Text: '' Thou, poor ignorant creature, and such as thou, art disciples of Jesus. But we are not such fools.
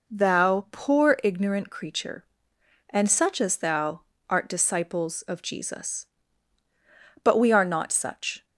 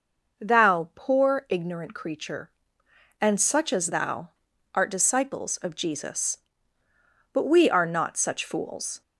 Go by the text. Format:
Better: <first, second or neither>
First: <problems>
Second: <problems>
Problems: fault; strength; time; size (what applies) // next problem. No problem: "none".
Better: second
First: stops before "fools"; at 8.4 s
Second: none